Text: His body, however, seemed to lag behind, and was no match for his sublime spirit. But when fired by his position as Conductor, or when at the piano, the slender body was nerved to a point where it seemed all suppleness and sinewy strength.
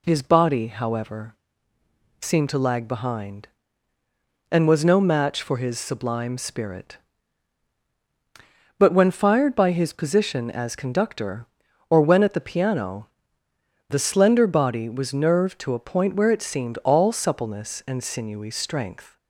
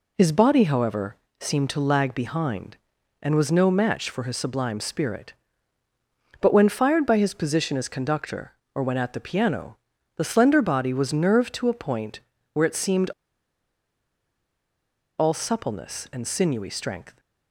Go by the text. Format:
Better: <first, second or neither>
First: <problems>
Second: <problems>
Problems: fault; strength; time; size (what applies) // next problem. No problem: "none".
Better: first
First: none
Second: pauses between "point" and "where"; slight; at 12.1 s; 0.34 s long // pauses between "seemed" and "all"; strong; at 13.0 s; 2.0 s long